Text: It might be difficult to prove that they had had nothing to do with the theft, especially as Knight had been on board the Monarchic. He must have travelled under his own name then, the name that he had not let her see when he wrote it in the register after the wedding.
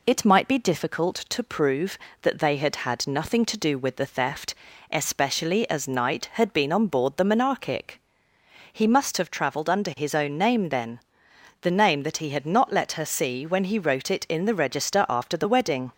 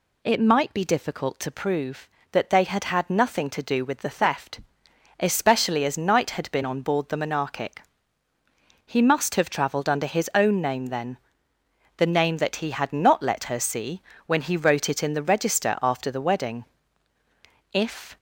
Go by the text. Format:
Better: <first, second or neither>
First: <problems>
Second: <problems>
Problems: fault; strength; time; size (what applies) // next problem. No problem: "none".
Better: first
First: none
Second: pauses between "see" and "when"; slight; at 14.0 s; 0.26 s long // goes on to say "If"; slight; from 17.7 s on; 0.44 s long